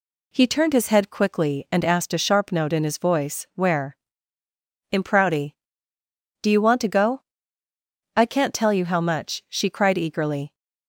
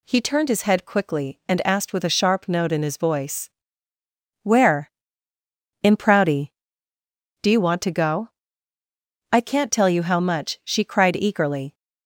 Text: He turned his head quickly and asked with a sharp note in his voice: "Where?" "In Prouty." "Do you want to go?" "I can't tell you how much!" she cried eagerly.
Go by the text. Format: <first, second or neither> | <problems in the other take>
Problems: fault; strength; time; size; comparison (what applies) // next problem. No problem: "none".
second | skips "with"; at 2.1 s